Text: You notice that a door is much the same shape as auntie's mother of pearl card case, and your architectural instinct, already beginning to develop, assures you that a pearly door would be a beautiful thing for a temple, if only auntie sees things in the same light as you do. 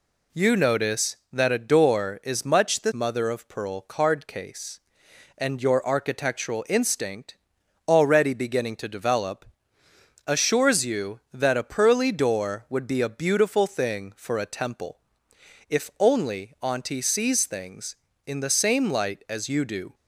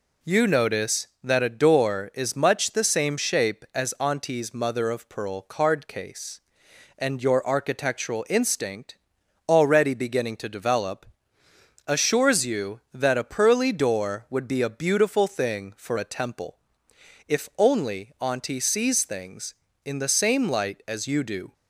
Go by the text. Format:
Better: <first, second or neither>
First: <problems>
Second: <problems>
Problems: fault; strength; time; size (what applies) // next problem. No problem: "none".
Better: second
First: skips "same shape as auntie's"; at 2.9 s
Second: none